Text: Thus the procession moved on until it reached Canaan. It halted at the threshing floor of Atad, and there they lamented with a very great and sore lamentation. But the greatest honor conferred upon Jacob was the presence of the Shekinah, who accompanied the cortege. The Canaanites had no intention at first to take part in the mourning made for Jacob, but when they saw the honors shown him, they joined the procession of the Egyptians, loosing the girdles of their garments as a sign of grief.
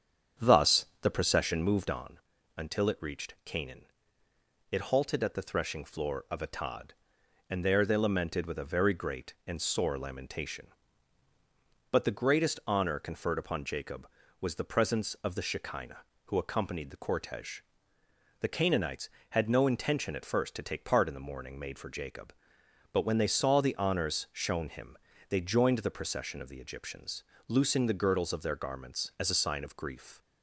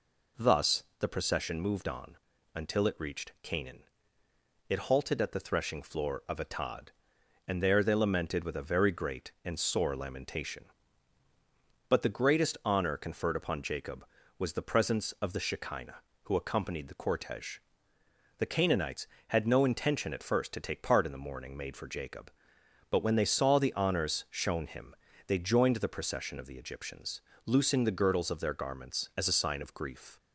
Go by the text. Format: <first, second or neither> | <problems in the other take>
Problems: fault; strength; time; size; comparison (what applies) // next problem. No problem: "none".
second | starts louder than the rest; strong; until 2.1 s; 8 dB // pauses between "Thus" and "the"; slight; at 0.8 s; 0.16 s long; slight in the second // pauses between "on" and "until"; at 2.1 s; 0.38 s long; also in the second